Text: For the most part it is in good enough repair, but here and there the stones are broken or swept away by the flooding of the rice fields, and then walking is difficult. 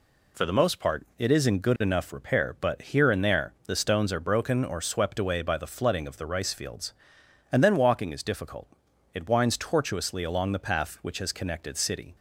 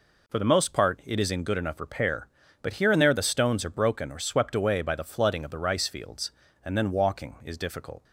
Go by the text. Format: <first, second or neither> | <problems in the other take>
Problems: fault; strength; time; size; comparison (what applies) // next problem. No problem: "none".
second | pauses between "there" and "the"; slight; at 3.5 s; 0.16 s long // goes on to say "It winds tortuously along the path which has connected city"; strong; from 9.1 s on; 3.0 s long